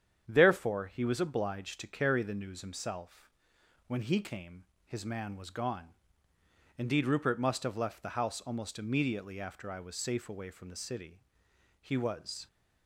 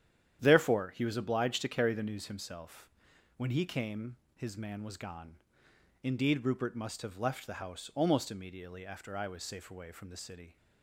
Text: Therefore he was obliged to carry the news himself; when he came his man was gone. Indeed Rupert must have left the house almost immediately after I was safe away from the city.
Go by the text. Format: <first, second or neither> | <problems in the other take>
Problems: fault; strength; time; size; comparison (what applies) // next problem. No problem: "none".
second | starts louder than the rest; strong; until 1.2 s; 8.5 dB; strong in the second // pauses between "came" and "his"; slight; at 4.6 s; 0.22 s long; slight in the second // goes on to say "He was"; noticeable; from 11.8 s on; 0.66 s long